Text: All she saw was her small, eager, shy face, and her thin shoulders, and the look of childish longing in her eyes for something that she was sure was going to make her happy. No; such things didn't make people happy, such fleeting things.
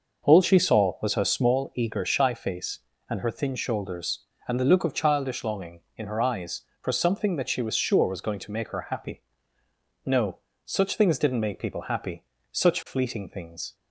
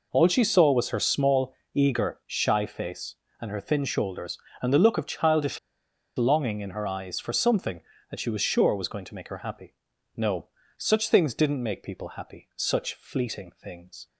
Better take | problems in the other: first | pauses between "childish" and "longing"; noticeable; at 5.5 s; 0.58 s long

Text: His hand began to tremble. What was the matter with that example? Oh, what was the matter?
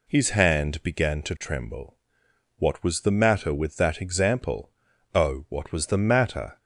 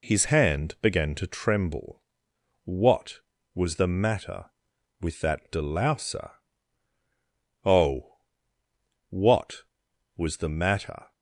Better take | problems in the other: first | says "delouser" for "example"; at 5.5 s

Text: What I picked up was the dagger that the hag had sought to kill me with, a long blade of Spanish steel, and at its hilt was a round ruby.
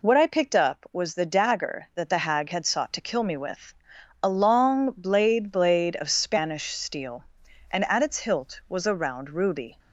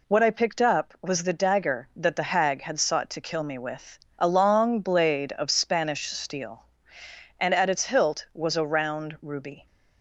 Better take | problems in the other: second | says "blade" twice; at 5.5 s

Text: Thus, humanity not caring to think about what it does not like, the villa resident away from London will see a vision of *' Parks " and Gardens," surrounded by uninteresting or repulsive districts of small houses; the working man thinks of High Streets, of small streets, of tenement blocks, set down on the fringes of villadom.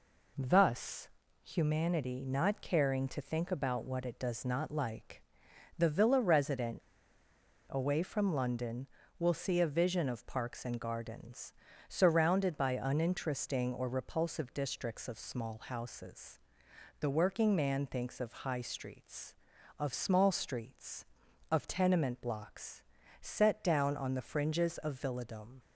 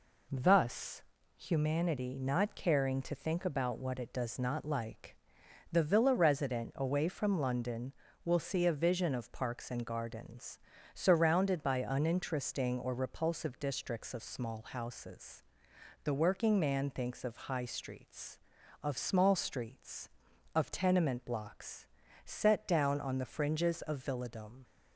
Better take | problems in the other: second | pauses between "resident" and "away"; noticeable; at 6.8 s; 0.88 s long

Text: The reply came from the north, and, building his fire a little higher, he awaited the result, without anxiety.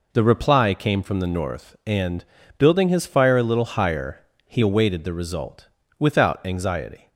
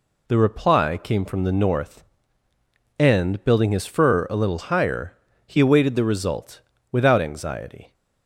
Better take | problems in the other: first | says "fur" for "fire"; at 3.8 s

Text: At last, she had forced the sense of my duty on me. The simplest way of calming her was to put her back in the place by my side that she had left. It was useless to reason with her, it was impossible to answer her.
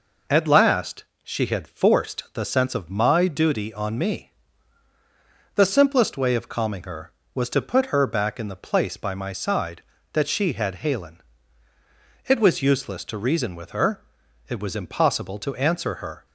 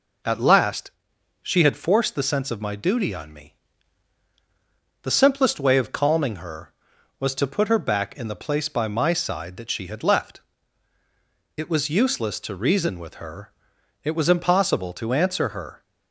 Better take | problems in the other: second | says "halen" for "left"; at 10.7 s

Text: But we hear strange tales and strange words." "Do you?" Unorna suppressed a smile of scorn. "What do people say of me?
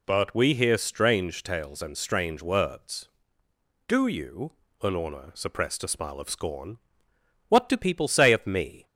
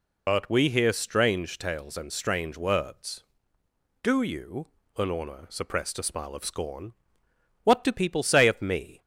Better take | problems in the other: first | loses the start of "But"; at 0.2 s; 60 ms

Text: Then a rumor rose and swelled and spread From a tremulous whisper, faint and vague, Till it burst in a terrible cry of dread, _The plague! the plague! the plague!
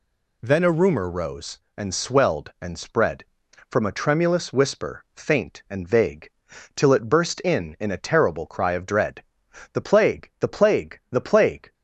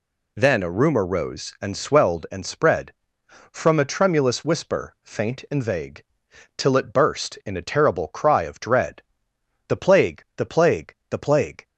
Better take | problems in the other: second | says "in" twice; at 7.7 s

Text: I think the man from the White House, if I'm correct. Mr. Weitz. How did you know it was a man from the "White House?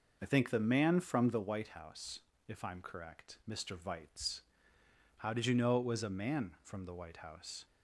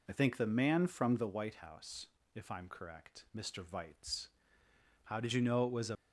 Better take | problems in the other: first | stops before "man from the White House"; at 5.9 s

